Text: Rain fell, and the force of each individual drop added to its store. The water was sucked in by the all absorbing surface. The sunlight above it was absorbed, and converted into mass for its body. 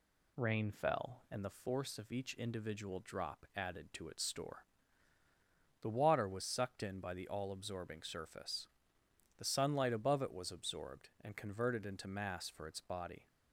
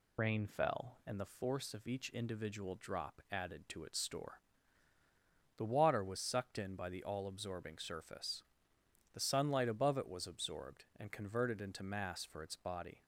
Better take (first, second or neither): first